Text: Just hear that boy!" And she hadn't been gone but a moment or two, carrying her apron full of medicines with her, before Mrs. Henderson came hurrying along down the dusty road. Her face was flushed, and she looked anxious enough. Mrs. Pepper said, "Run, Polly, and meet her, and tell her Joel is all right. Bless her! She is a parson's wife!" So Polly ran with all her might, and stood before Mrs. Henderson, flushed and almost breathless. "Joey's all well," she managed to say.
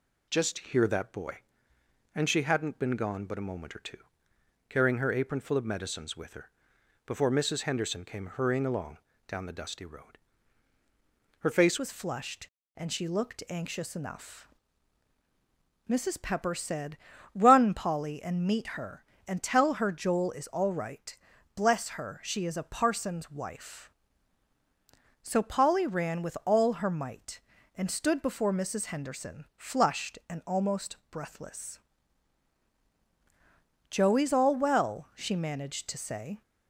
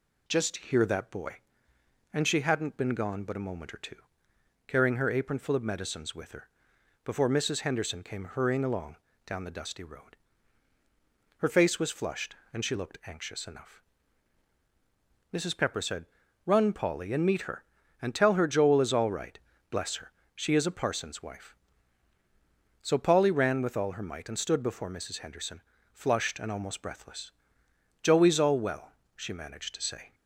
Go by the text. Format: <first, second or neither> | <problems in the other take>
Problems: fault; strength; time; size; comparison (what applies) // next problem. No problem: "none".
second | pauses between "along" and "down"; slight; at 8.9 s; 0.28 s long; slight in the second // changes voice at "was"; from 11.7 s on; 24.7 s long